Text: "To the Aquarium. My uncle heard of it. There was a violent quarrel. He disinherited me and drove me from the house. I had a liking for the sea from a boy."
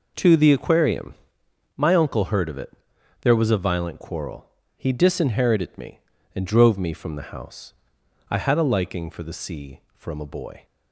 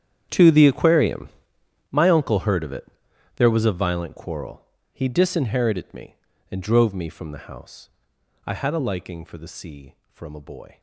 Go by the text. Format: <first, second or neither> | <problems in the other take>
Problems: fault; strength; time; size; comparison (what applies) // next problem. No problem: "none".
first | gets quieter; strong; throughout; 19 dB